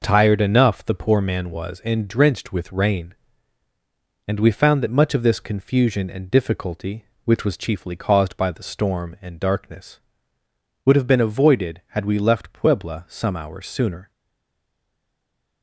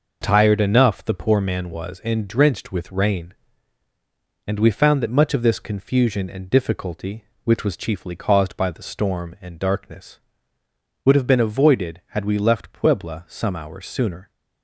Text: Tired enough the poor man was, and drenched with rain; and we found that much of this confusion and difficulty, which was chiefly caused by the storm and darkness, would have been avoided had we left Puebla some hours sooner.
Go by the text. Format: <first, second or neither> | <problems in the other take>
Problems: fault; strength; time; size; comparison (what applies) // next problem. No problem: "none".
second | stays silent after the last word; noticeable; from 14.1 s on; 1.5 s long